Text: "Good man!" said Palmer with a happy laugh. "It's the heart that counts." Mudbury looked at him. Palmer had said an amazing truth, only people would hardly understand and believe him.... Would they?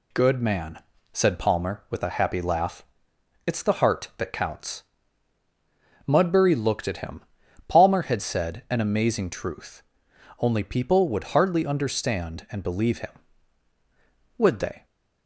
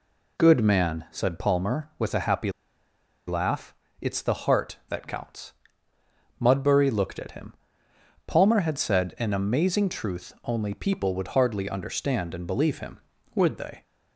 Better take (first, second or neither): first